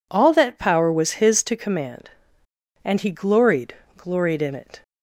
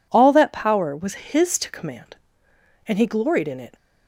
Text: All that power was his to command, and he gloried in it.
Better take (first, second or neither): second